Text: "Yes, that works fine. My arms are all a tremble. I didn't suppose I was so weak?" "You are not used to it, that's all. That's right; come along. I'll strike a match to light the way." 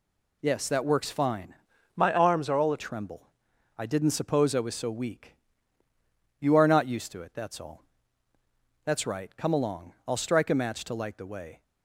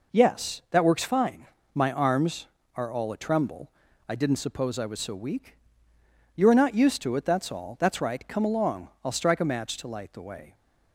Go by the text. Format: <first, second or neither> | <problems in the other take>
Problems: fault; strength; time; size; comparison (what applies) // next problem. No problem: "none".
second | changes voice from "My" to "a"; from 1.9 to 2.7 s; 0.8 s long